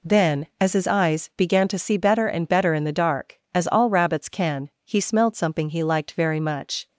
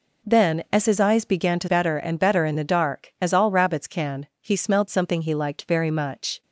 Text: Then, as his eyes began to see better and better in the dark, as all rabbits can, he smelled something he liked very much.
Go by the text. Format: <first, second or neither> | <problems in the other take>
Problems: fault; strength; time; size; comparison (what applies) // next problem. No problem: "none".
first | skips "see"; at 1.6 s